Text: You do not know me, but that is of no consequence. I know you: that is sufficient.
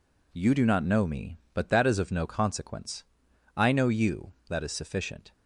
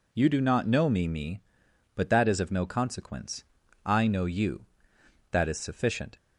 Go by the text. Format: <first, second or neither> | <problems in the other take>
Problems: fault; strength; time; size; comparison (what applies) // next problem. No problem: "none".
first | says "me" twice; at 1.0 s